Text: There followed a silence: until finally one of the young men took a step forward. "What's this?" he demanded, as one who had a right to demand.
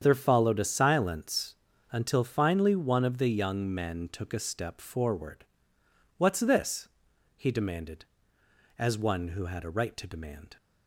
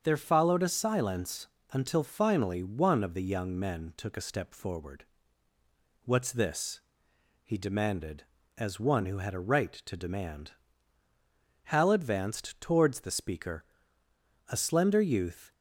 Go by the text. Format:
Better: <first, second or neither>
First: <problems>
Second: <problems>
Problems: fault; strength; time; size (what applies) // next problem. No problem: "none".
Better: first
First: starts louder than the rest; strong; until 1.0 s; 8 dB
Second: starts louder than the rest; until 1.0 s; 7 dB // goes on to say "Hal advanced towards the speaker a slender youth"; strong; from 11.6 s on; 3.8 s long